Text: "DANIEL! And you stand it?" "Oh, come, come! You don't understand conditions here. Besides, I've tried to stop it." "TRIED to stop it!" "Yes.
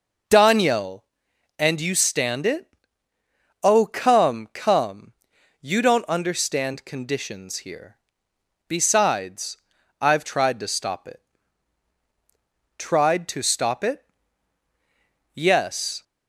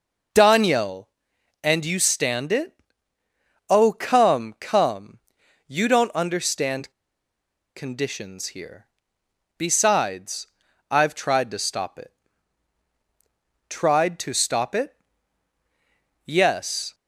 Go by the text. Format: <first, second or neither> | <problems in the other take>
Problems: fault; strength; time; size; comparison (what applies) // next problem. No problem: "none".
first | pauses between "understand" and "conditions"; noticeable; at 6.9 s; 0.83 s long